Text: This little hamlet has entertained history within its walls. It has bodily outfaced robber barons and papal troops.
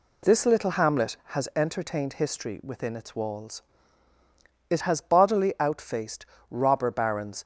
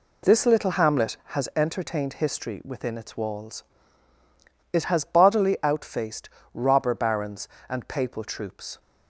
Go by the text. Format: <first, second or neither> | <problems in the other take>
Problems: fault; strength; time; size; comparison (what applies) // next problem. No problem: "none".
second | pauses between "outfaced" and "robber"; slight; at 6.2 s; 0.22 s long; slight in the second // stops before "and papal troops"; at 7.4 s